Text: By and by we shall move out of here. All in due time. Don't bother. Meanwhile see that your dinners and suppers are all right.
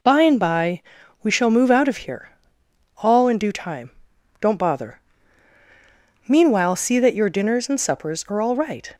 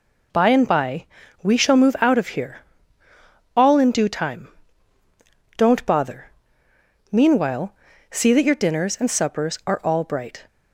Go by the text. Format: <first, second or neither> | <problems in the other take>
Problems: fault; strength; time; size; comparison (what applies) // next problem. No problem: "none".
first | pauses between "by" and "we"; slight; at 1.0 s; 0.36 s long; also in the first // pauses between "Meanwhile" and "see"; at 7.7 s; 0.38 s long // says "bright" for "right"; at 10.0 s